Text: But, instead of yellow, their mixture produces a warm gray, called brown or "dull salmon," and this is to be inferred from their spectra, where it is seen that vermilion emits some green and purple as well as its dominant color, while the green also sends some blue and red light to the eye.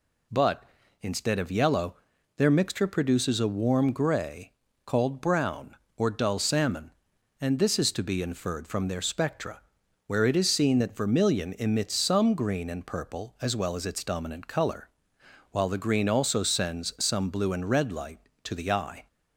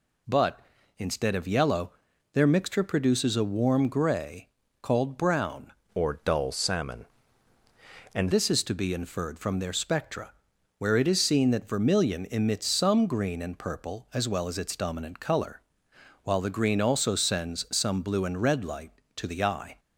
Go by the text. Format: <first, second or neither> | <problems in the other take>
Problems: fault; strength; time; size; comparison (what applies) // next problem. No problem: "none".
first | changes voice from "or" to "and"; from 5.9 to 8.3 s; 2.4 s long